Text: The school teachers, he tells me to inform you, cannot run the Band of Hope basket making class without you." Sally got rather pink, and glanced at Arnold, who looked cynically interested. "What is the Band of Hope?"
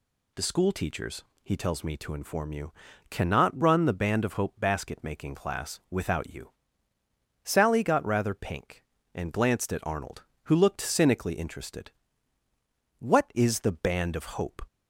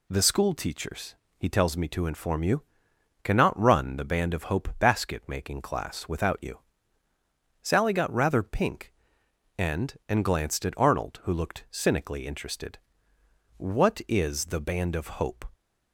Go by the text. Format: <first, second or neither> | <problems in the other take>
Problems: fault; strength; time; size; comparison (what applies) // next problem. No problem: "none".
first | says "and" twice; at 10.0 s